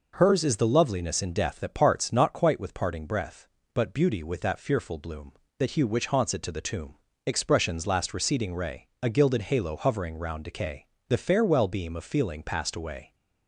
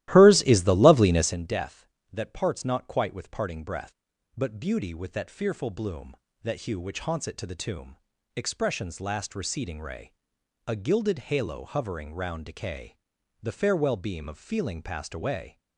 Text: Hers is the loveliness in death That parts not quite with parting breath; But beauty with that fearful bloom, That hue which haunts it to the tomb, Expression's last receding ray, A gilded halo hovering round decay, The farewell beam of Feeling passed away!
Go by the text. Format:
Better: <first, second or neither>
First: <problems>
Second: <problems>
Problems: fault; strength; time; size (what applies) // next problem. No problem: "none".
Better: first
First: none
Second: starts louder than the rest; strong; until 1.4 s; 15 dB